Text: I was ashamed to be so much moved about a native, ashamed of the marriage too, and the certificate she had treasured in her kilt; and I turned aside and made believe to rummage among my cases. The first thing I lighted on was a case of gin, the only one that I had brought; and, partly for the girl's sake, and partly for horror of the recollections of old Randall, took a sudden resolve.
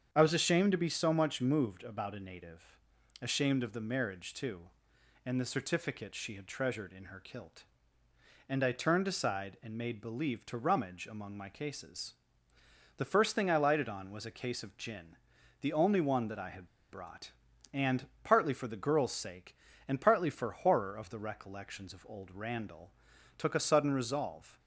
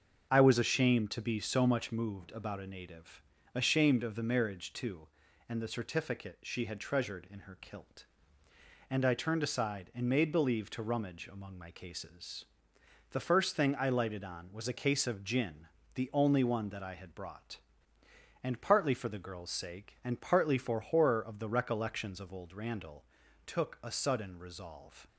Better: second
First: starts louder than the rest; strong; until 1.1 s; 7.5 dB // pauses between "had" and "brought"; slight; at 16.6 s; 0.24 s long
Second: starts louder than the rest; until 1.3 s; 6.5 dB

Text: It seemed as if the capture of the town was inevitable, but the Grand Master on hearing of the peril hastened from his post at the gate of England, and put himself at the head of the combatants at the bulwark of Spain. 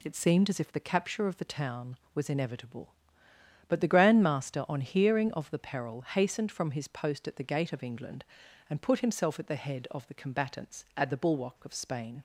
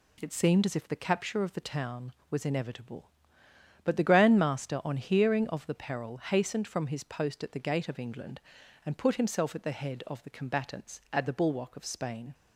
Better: neither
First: none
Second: none

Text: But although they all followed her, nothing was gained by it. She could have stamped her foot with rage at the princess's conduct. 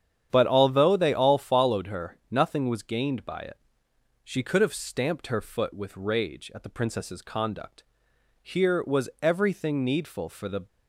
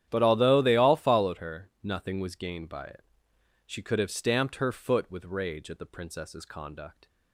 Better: second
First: starts louder than the rest; strong; until 1.3 s; 9 dB // goes on to say "Here was everything needful for the"; strong; from 8.4 s on; 2.2 s long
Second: starts louder than the rest; strong; until 1.1 s; 10.5 dB

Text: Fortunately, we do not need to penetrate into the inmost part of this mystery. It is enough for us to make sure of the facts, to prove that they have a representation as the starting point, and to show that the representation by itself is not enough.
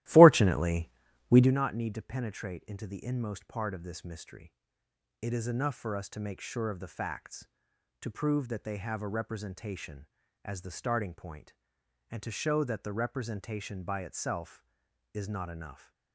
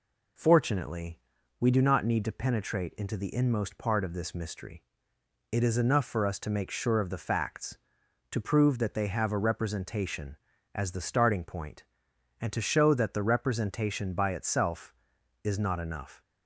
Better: second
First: starts louder than the rest; strong; until 1.6 s; 15.5 dB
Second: none

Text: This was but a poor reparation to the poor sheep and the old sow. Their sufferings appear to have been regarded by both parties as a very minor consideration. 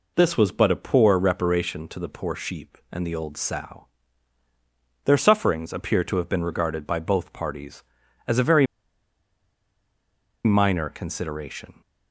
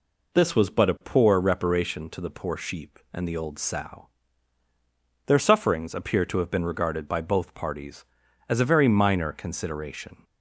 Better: second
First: pauses between "very" and "minor"; strong; at 8.6 s; 1.7 s long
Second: none

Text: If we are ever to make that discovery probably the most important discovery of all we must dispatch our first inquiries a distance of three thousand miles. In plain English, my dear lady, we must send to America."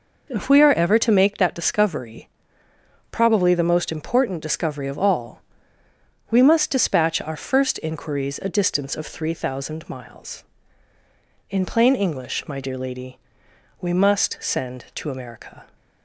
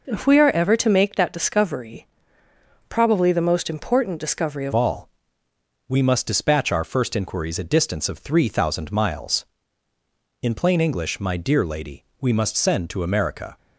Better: first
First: pauses between "discovery" and "probably"; noticeable; at 2.2 s; 0.82 s long // pauses between "all" and "we"; noticeable; at 5.4 s; 0.90 s long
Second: pauses between "discovery" and "probably"; noticeable; at 2.0 s; 0.82 s long // changes voice at "all"; from 4.7 s on; 8.8 s long // pauses between "all" and "we"; noticeable; at 5.0 s; 0.80 s long

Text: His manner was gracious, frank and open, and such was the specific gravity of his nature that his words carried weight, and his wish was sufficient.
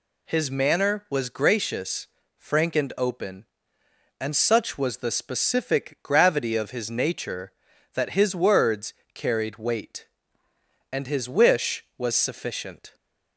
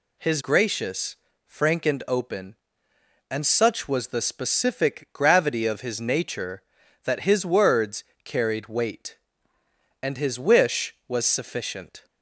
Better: first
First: pauses between "words" and "carried"; slight; at 8.9 s; 0.18 s long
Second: skips "manner was"; at 0.4 s // pauses between "words" and "carried"; slight; at 8.0 s; 0.18 s long

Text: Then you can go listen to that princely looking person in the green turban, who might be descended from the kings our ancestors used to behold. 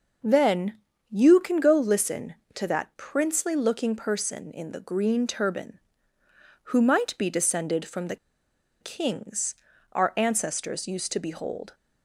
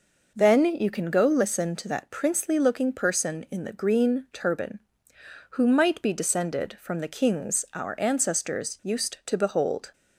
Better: second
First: pauses between "Then" and "you"; slight; at 0.7 s; 0.32 s long // pauses between "the" and "kings"; noticeable; at 8.1 s; 0.64 s long // pauses between "kings" and "our"; at 9.5 s; 0.38 s long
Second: none

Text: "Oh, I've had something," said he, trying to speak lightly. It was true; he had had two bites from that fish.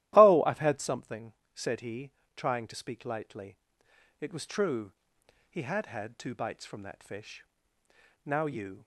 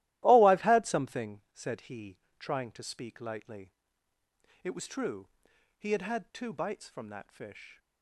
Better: second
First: starts louder than the rest; strong; until 1.1 s; 14 dB // goes on to say "Now you"; noticeable; from 8.2 s on; 0.62 s long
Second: starts louder than the rest; strong; until 1.2 s; 15.5 dB

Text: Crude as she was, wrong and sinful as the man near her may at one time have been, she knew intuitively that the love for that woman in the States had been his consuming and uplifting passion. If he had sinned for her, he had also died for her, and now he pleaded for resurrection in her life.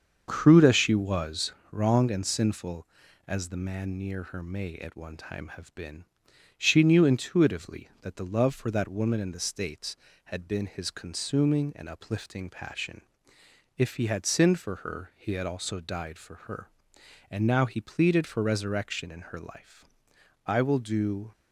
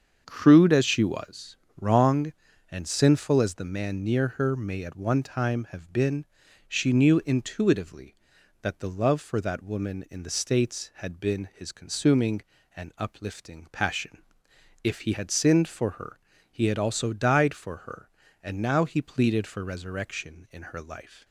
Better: second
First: starts louder than the rest; until 1.2 s; 7 dB // goes on to say "I will do"; noticeable; from 20.4 s on; 0.86 s long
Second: starts louder than the rest; until 1.2 s; 7 dB

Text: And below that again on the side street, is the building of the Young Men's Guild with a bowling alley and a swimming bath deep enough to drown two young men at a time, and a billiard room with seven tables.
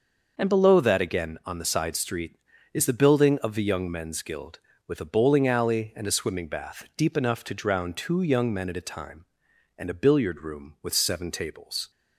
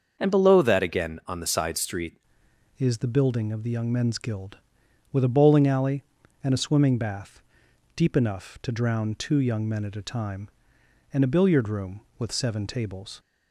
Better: first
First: starts louder than the rest; noticeable; until 1.3 s; 6 dB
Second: starts louder than the rest; until 1.2 s; 6.5 dB // changes voice at "is"; from 2.7 s on; 10.4 s long // pauses between "bath" and "deep"; noticeable; at 7.3 s; 0.58 s long

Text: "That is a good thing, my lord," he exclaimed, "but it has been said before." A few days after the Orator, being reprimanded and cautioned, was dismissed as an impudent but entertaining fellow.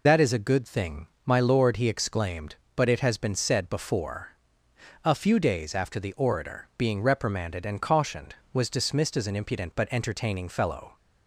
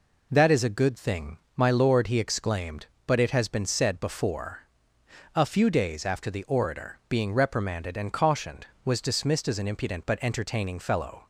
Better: second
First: loses the start of "That"; at 0.0 s; 55 ms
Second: none

